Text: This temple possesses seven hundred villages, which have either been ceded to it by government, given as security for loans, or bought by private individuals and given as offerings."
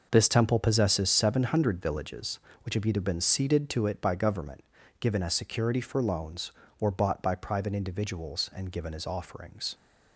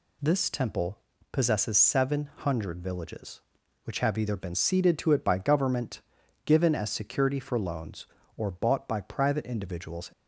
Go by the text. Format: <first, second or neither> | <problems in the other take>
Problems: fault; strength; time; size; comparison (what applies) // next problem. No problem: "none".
first | pauses between "temple" and "possesses"; slight; at 0.9 s; 0.32 s long // stops before "and given as offerings"; at 10.1 s